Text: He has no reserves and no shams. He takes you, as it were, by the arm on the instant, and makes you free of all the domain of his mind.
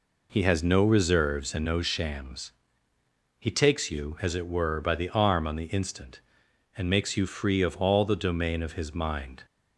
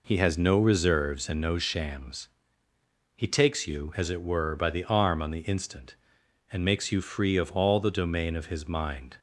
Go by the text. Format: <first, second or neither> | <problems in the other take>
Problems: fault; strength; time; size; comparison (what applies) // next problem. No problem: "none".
neither | none